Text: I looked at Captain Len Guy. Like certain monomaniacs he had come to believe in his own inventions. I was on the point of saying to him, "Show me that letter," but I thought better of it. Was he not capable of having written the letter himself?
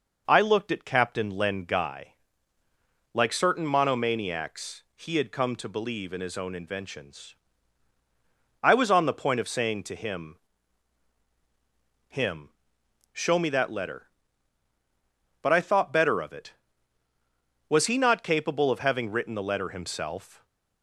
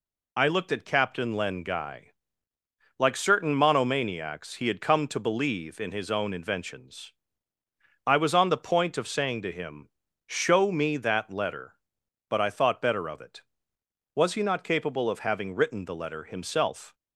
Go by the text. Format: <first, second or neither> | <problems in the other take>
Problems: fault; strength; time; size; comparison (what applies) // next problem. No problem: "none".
second | says "him" twice; at 12.0 s